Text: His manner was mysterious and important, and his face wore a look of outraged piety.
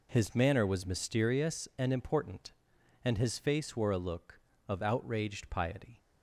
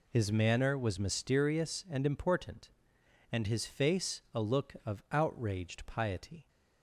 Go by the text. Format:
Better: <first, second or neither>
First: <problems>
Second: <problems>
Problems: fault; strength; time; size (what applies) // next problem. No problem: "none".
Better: first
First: none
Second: skips "wore"; at 4.2 s